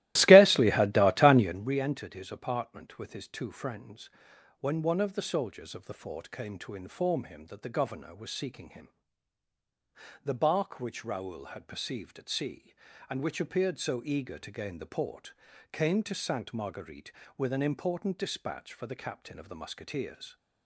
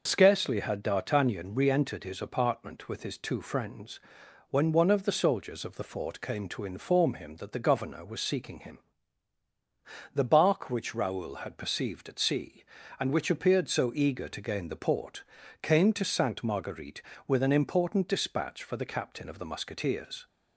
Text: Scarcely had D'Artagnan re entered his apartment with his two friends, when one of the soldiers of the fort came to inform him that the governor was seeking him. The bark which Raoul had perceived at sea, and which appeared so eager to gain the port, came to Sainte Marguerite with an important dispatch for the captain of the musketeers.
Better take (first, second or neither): second